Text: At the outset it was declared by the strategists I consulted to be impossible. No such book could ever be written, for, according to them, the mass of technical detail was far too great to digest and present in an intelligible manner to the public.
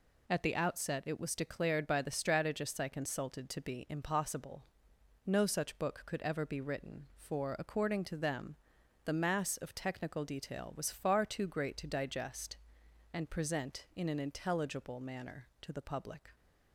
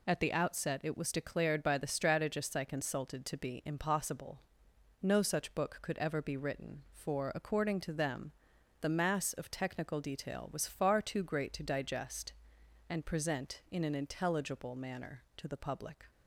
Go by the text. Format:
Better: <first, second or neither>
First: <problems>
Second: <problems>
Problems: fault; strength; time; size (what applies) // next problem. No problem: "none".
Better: neither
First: none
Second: none